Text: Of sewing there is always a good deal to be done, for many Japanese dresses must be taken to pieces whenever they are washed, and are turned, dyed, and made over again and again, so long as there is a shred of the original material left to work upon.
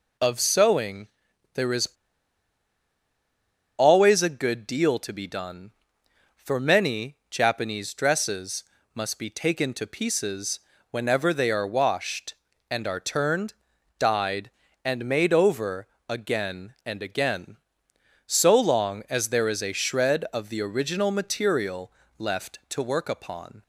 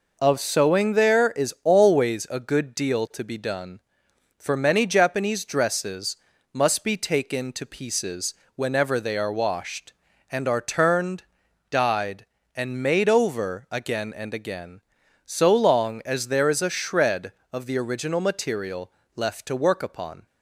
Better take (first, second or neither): second